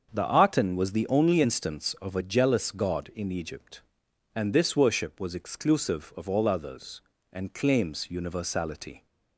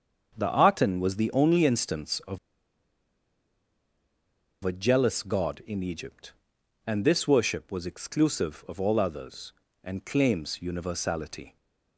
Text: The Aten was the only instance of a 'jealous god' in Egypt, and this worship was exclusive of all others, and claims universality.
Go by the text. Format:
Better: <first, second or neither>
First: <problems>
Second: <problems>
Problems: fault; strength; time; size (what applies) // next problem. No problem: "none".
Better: first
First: starts louder than the rest; until 1.1 s; 6.5 dB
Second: starts louder than the rest; until 1.3 s; 6.5 dB // pauses between "of" and "a"; strong; at 2.3 s; 2.2 s long